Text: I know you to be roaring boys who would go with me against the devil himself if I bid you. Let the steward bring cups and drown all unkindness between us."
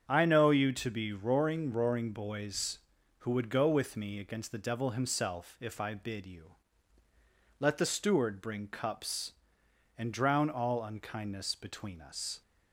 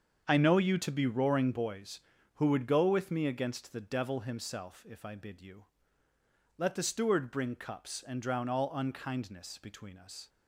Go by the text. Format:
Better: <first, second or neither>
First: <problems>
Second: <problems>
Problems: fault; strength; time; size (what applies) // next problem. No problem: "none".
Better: second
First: starts louder than the rest; strong; until 1.0 s; 7.5 dB // says "roaring" twice; at 1.7 s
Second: starts louder than the rest; strong; until 1.2 s; 7 dB